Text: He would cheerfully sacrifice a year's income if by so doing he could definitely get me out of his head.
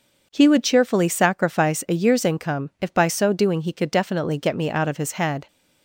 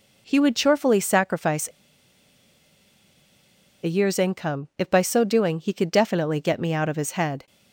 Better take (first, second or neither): first